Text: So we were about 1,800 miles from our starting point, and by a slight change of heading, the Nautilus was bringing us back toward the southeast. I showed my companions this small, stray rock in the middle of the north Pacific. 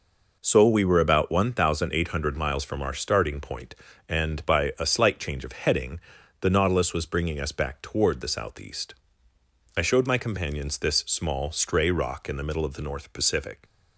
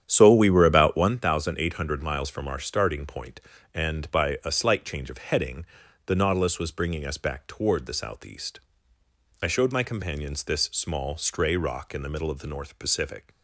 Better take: first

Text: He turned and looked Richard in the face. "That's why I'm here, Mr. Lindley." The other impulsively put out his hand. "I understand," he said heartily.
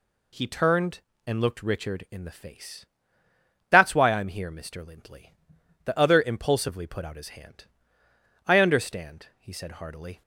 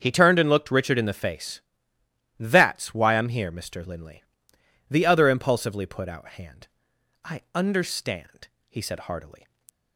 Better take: first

